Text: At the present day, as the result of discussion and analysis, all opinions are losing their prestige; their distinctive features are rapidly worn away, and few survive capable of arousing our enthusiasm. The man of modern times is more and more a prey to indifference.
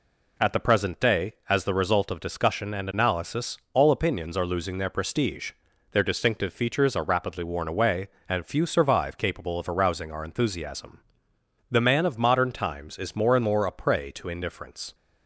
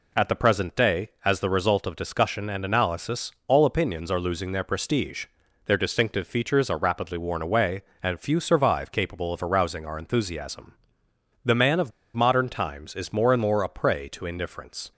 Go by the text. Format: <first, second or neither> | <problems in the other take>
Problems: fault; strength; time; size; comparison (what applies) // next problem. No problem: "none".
first | pauses between "of" and "modern"; slight; at 11.9 s; 0.24 s long